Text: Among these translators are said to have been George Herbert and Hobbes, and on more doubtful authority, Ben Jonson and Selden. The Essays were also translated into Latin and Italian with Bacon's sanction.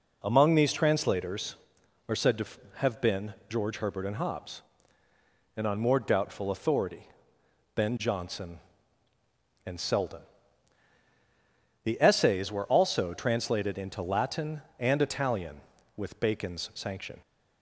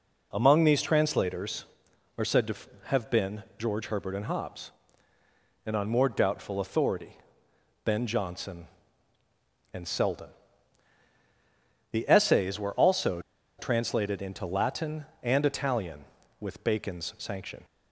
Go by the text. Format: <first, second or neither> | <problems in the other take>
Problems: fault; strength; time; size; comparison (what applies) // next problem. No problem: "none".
first | pauses between "been" and "George"; slight; at 3.4 s; 0.16 s long; slight in the first // pauses between "also" and "translated"; at 13.1 s; 0.38 s long